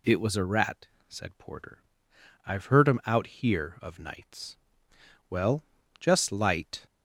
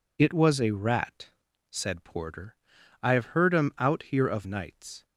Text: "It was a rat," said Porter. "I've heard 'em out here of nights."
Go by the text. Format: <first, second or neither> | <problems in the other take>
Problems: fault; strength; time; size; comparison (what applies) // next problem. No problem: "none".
second | goes on to say "Well just light"; from 5.3 s on; 1.5 s long